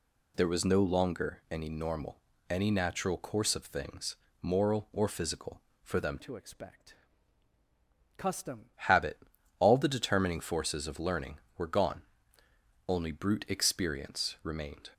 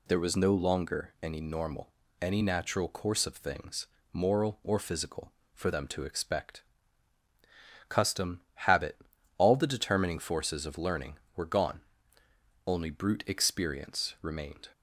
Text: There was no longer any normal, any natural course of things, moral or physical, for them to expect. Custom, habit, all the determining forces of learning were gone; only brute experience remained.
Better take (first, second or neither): second